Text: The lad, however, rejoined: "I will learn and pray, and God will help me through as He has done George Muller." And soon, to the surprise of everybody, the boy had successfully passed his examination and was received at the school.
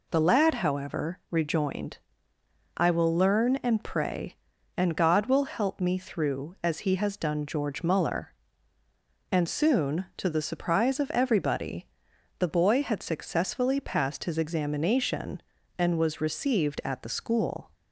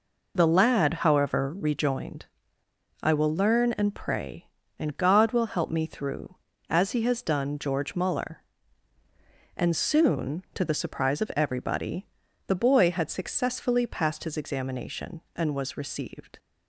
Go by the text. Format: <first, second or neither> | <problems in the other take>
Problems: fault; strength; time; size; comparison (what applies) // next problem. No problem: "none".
first | stops before "at the school"; at 16.3 s